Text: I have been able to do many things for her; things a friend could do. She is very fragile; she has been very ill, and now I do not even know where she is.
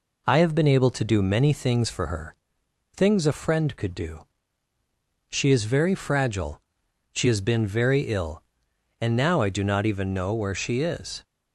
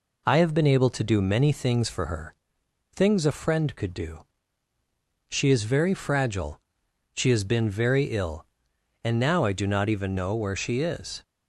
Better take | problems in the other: neither | none

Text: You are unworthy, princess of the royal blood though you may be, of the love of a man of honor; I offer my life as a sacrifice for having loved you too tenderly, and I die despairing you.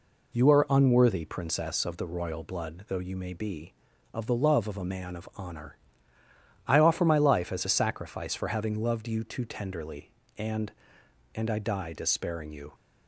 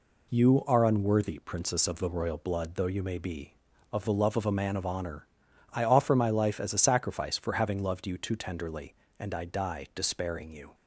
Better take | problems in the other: second | says "and" twice; at 11.3 s

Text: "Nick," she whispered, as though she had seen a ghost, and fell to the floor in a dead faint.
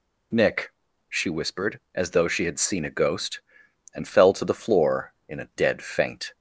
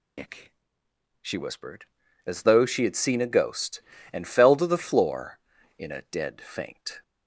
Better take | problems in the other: first | loses the start of "Nick"; at 0.1 s; 75 ms

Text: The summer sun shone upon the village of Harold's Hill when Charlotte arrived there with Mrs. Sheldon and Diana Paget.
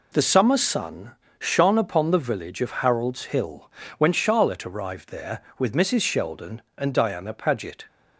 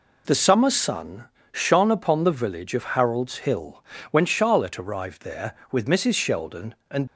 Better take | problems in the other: first | pauses between "sun" and "shone"; slight; at 1.2 s; 0.26 s long; slight in the first // pauses between "Hill" and "when"; slight; at 3.8 s; 0.26 s long; slight in the first // stops before "Diana Paget"; at 7.0 s

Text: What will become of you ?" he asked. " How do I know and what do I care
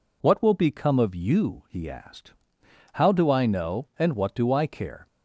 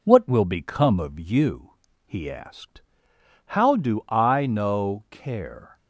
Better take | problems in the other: first | skips "and what do I"; at 5.0 s

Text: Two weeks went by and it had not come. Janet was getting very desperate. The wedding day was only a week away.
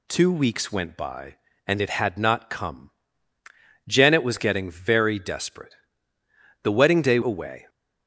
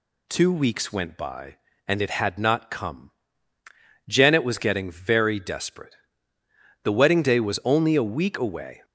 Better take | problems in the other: second | skips "was only a week"; at 7.2 s

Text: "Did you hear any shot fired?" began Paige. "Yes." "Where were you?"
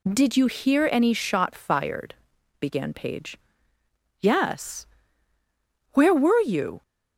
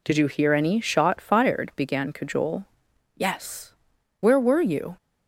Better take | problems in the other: first | says "Cajole" for "Paige"; at 2.1 s

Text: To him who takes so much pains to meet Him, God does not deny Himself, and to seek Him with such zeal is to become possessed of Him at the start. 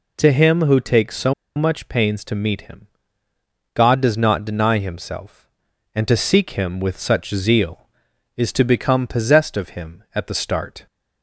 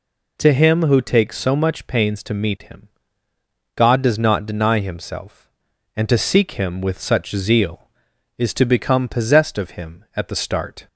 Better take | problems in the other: second | pauses between "so" and "much"; slight; at 1.3 s; 0.22 s long

